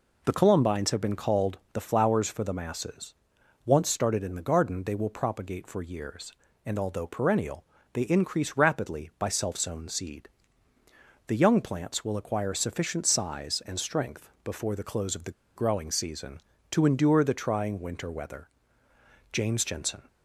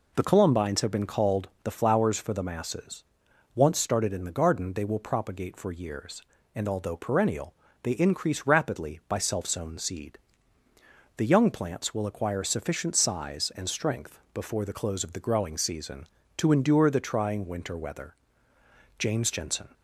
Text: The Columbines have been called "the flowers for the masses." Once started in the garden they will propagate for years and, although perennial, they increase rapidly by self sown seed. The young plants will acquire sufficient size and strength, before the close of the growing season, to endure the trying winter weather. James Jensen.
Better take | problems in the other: second | pauses between "the" and "growing"; slight; at 15.3 s; 0.25 s long

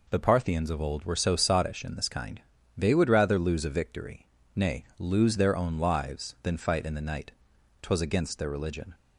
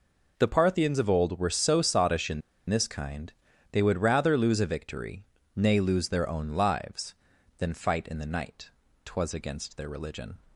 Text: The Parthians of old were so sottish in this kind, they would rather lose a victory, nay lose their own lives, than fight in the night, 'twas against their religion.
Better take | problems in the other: first | pauses between "in" and "this"; slight; at 2.4 s; 0.28 s long

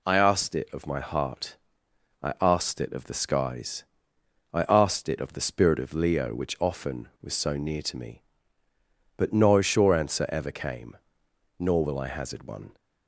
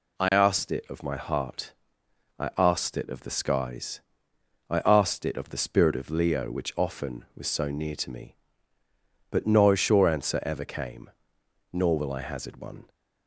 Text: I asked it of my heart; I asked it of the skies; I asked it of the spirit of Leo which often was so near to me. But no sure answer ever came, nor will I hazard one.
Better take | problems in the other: neither | none

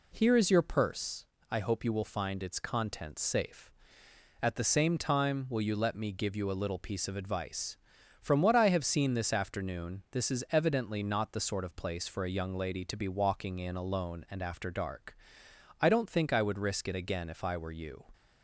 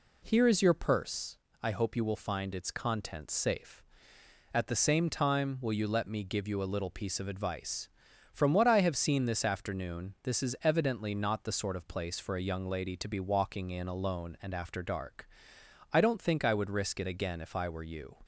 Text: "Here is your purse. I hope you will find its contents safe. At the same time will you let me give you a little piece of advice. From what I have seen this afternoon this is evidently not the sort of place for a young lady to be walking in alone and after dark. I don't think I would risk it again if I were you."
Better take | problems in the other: neither | none

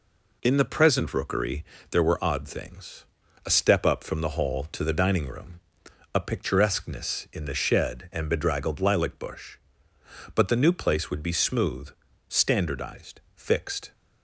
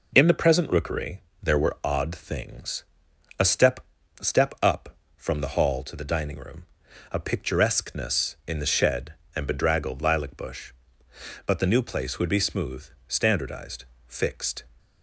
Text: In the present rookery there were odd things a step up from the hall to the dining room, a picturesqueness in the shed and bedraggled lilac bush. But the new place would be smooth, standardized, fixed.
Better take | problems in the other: first | pauses between "rookery" and "there"; slight; at 1.2 s; 0.20 s long; slight in the first // pauses between "things" and "a"; noticeable; at 2.8 s; 0.56 s long; also in the first // says "step" twice; at 4.2 s

